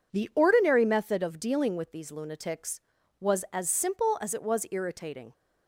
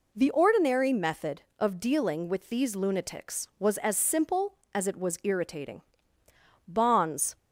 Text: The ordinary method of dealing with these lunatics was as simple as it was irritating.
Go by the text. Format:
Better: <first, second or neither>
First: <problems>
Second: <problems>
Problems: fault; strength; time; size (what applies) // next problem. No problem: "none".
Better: first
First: none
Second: goes on to say "Bonds"; noticeable; from 6.6 s on; 0.70 s long